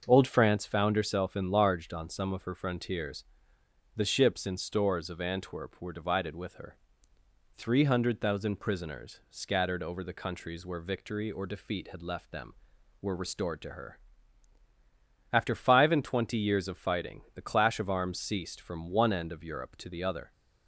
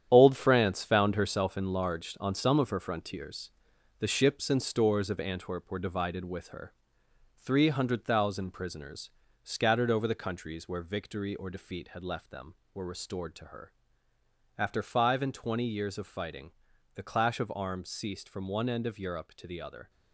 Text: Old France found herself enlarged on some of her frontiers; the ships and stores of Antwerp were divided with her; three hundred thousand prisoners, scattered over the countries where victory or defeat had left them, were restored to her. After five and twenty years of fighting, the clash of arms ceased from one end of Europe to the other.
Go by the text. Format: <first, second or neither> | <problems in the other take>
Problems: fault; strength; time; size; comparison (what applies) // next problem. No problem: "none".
first | gets quieter; strong; throughout; 9 dB // starts louder than the rest; strong; until 1.1 s; 9.5 dB; also in the first